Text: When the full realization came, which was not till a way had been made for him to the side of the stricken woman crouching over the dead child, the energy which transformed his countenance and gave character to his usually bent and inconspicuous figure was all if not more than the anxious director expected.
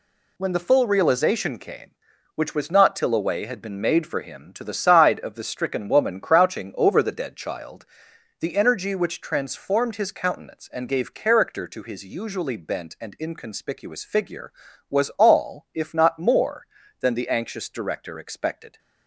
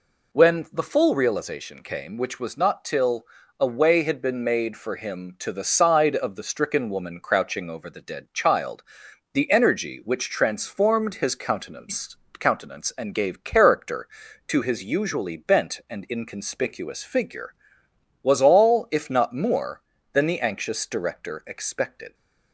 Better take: first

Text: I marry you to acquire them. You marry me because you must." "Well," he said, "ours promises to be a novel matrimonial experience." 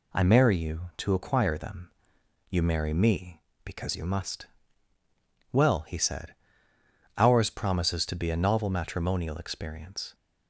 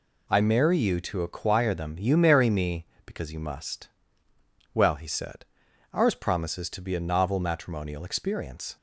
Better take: neither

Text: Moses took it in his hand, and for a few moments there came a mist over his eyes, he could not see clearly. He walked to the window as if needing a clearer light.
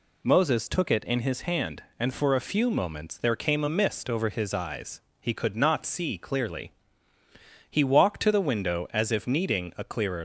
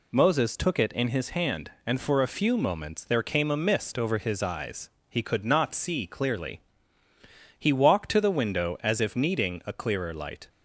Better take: second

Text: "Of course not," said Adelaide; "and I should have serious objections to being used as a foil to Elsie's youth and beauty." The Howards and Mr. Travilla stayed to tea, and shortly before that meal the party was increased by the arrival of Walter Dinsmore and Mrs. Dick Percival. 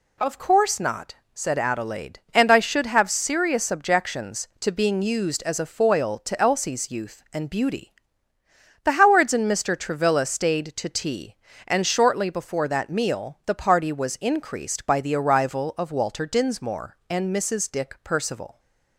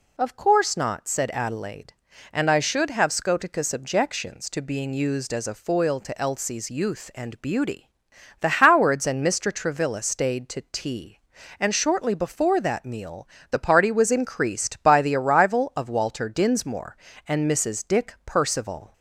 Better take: first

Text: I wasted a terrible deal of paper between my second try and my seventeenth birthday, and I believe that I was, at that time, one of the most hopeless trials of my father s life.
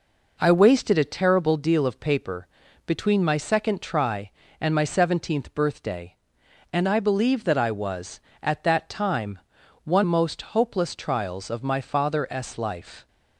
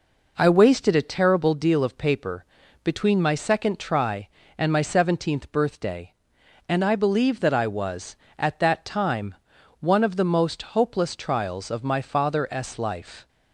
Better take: second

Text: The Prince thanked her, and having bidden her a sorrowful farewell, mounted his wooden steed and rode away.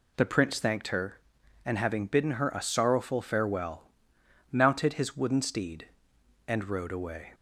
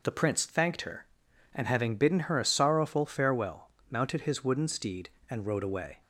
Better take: neither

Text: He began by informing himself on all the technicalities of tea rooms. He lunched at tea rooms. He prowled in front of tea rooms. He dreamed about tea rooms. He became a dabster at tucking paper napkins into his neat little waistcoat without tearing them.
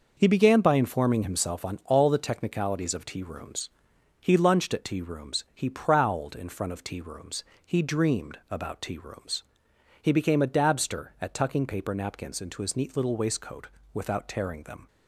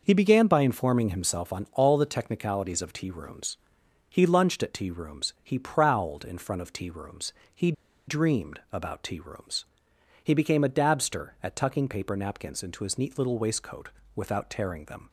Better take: first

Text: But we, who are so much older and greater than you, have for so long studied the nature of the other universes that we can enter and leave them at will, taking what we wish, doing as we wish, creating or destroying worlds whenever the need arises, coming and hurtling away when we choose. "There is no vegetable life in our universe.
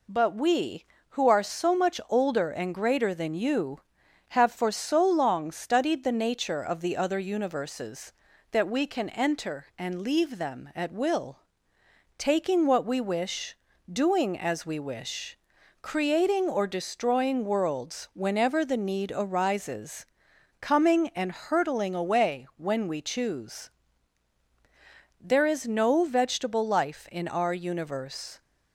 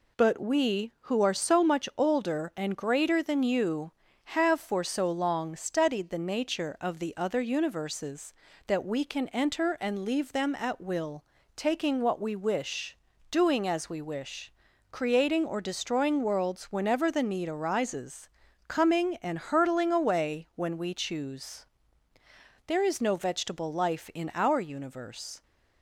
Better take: neither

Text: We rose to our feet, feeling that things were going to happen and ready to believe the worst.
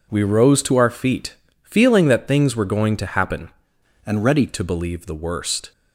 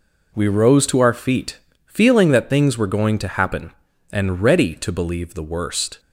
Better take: second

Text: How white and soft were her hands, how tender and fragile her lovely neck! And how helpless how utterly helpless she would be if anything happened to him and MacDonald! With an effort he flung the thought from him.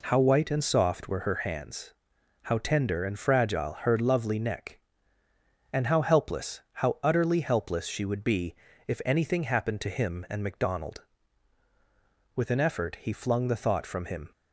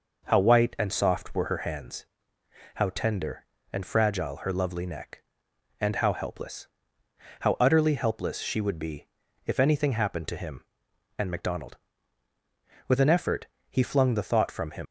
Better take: first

